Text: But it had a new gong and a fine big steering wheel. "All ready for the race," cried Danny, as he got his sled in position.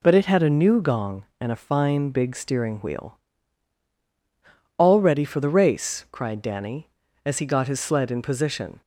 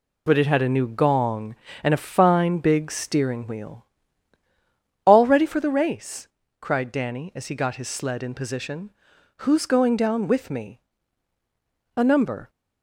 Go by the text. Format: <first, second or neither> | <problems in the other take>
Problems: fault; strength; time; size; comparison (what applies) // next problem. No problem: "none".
first | goes on to say "Who's going down with me A number"; strong; from 9.4 s on; 3.0 s long